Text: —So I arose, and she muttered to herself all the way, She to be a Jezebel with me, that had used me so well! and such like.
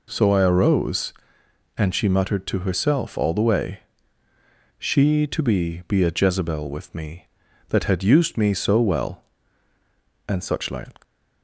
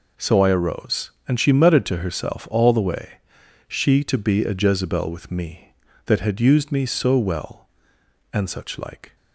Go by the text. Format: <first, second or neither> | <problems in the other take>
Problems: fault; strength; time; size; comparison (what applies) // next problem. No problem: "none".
second | says "be" twice; at 5.8 s